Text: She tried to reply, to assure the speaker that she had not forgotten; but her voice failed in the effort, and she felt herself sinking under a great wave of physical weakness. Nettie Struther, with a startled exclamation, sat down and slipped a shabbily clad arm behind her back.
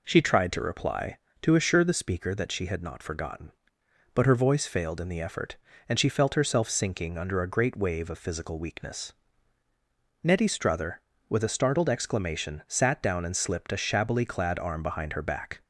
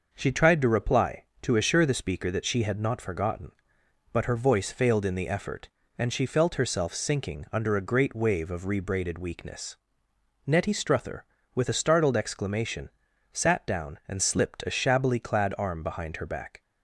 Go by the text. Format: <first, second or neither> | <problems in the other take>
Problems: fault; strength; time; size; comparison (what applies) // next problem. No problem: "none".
first | says "rebraided" for "physical"; at 8.6 s